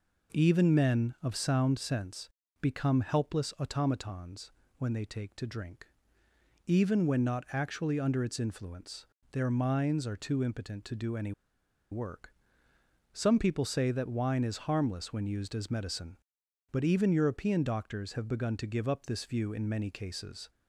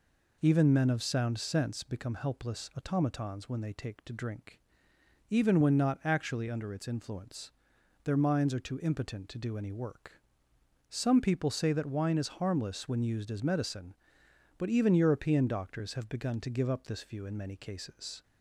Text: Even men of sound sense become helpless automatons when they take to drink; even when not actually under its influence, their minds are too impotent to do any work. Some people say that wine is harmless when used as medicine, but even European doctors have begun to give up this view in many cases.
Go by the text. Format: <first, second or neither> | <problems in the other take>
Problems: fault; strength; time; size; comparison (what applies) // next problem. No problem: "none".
second | pauses between "sense" and "become"; slight; at 2.2 s; 0.32 s long // pauses between "automatons" and "when"; slight; at 4.5 s; 0.26 s long // pauses between "any" and "work"; noticeable; at 11.3 s; 0.59 s long